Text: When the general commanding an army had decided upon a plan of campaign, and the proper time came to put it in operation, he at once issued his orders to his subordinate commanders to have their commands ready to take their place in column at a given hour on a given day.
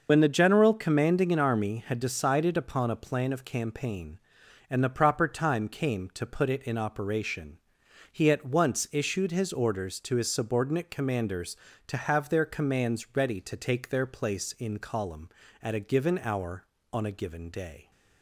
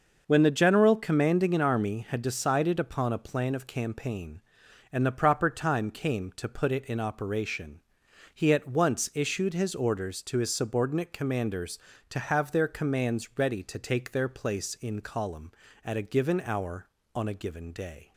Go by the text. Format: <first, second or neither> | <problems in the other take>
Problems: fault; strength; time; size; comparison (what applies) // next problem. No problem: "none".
second | loses the start of "When"; at 0.0 s; 55 ms // starts louder than the rest; noticeable; until 1.1 s; 6 dB; noticeable in the second